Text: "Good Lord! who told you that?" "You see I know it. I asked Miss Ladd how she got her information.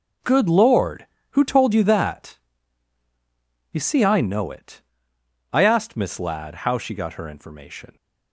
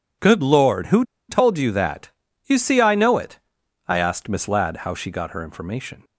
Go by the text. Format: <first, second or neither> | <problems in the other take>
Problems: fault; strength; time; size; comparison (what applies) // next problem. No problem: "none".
first | pauses between "who" and "told"; slight; at 1.0 s; 0.26 s long